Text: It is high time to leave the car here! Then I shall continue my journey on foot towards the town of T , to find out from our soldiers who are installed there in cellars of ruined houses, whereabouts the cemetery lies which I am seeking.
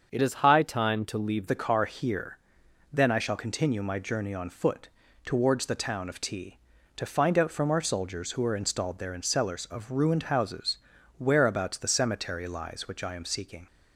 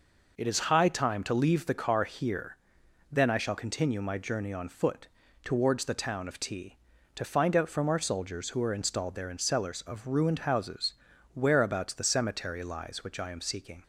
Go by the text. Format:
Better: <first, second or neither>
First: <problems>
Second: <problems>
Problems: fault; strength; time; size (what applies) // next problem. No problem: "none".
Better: second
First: starts louder than the rest; until 1.1 s; 6.5 dB // changes voice from "is" to "leave"; from 0.2 to 1.4 s; 1.2 s long // pauses between "foot" and "towards"; at 4.8 s; 0.38 s long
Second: pauses between "foot" and "towards"; at 5.0 s; 0.38 s long